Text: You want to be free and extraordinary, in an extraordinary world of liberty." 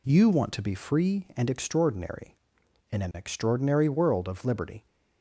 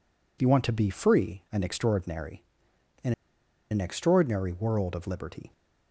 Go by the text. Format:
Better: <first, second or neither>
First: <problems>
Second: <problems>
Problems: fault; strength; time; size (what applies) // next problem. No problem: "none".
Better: first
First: none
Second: pauses between "in" and "an"; noticeable; at 3.1 s; 0.59 s long